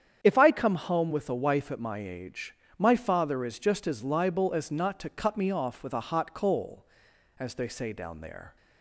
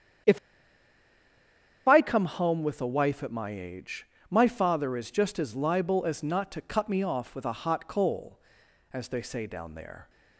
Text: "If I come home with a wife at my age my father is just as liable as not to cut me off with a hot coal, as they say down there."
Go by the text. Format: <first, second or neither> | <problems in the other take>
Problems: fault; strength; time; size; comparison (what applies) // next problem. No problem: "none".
first | starts louder than the rest; strong; until 2.7 s; 8.5 dB; strong in the first // pauses between "If" and "I"; strong; at 0.3 s; 1.4 s long // pauses between "age" and "my"; slight; at 4.0 s; 0.24 s long; slight in the first